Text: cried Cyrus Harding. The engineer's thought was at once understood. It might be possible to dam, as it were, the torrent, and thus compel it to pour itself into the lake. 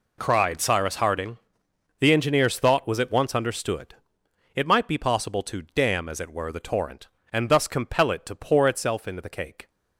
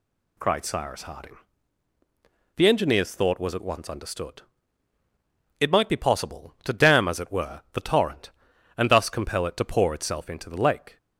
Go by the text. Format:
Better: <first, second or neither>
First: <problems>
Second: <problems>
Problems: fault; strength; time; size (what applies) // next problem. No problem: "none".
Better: second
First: says "cake" for "lake"; at 9.3 s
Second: none